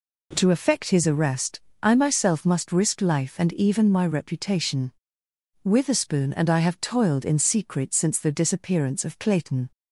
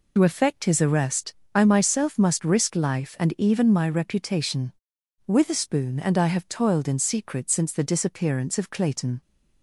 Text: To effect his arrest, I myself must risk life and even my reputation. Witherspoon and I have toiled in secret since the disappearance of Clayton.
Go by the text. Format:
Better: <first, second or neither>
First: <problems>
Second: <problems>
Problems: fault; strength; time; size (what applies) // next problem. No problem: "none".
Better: first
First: none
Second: loses the start of "To"; at 0.1 s; 65 ms